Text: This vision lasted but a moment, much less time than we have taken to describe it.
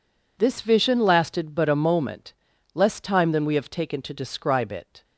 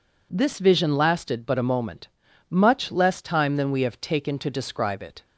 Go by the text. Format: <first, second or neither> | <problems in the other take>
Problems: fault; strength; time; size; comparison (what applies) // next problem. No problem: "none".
second | skips "much"; at 2.5 s